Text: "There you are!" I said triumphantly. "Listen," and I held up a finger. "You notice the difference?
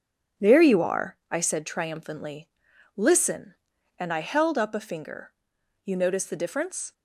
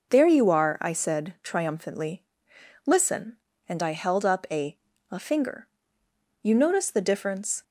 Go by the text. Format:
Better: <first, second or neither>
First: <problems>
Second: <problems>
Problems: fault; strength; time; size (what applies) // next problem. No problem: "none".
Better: first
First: none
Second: says "a" twice; at 5.1 s